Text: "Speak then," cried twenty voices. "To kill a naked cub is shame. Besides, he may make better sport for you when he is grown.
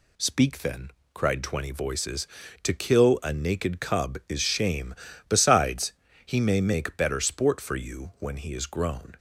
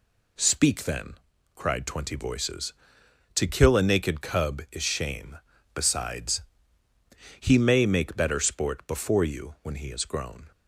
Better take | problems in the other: first | says "before" for "for"; at 8.8 s

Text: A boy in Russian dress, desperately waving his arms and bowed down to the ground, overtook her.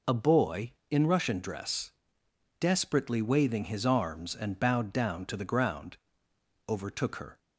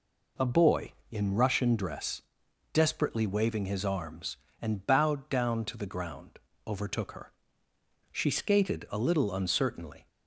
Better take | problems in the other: first | goes on to say "She skated a little uncertainly"; strong; from 8.1 s on; 1.9 s long

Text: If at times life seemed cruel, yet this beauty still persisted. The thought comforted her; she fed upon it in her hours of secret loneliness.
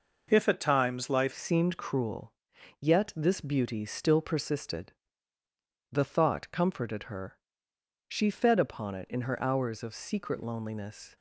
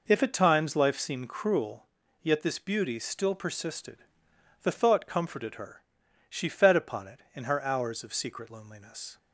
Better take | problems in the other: second | changes voice at "seemed"; from 1.3 s on; 9.8 s long

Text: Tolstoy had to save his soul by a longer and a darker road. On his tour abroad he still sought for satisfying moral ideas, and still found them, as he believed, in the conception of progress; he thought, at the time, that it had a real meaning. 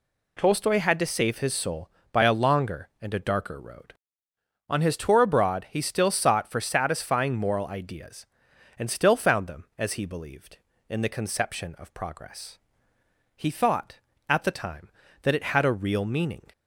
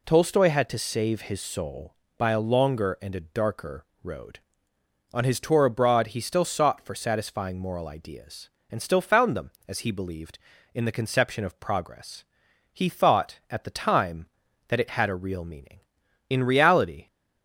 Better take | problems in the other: first | pauses between "darker" and "road"; slight; at 3.8 s; 0.18 s long // goes on to say "In reality"; noticeable; from 16.2 s on; 0.78 s long

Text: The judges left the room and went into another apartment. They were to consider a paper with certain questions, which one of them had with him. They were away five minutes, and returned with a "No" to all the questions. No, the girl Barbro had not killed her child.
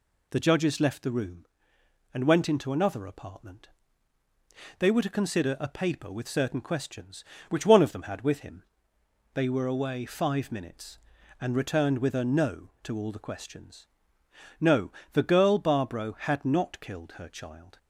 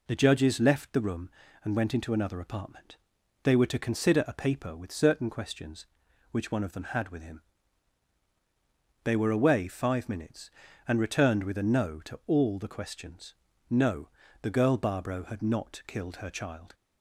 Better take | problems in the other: neither | none

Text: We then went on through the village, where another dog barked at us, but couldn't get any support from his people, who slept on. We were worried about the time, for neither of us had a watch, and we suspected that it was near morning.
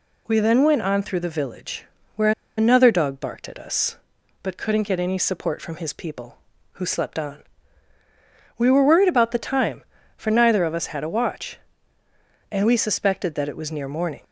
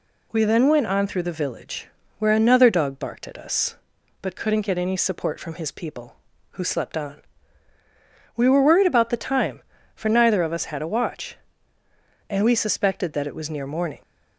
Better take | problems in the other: second | pauses between "where" and "another"; slight; at 2.3 s; 0.26 s long

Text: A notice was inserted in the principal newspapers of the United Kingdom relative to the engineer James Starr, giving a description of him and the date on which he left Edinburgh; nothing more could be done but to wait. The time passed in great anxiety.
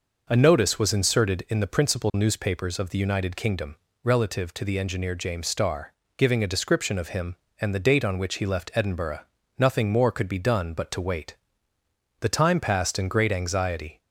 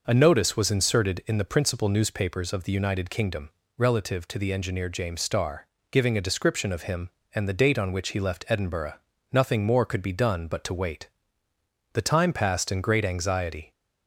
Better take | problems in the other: neither | pauses between "Kingdom" and "relative"; slight; the same in both

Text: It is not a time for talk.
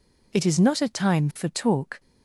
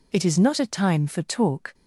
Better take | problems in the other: neither | none

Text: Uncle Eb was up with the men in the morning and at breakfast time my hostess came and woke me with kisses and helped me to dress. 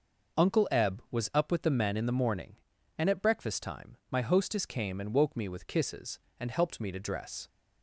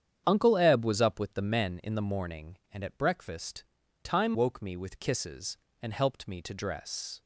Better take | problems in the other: first | starts louder than the rest; strong; until 1.2 s; 8.5 dB // pauses between "breakfast" and "time"; at 3.6 s; 0.40 s long // skips "my hostess came and"; at 4.3 s

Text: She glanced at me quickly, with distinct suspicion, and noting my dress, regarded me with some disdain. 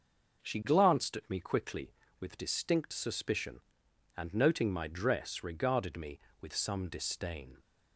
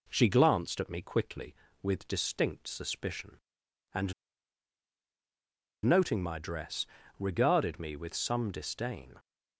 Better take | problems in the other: first | pauses between "and" and "noting"; strong; at 4.1 s; 1.7 s long

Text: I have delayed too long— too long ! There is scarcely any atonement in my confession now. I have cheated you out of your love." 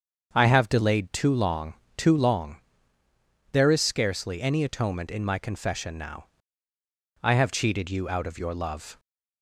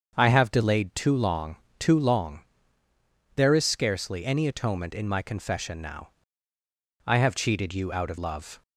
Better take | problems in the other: first | starts louder than the rest; until 1.1 s; 7 dB; also in the first // skips "your"; at 8.1 s

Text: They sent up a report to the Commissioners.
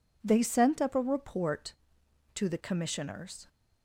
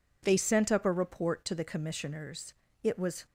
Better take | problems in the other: first | goes on to say "It was"; slight; from 2.8 s on; 0.42 s long

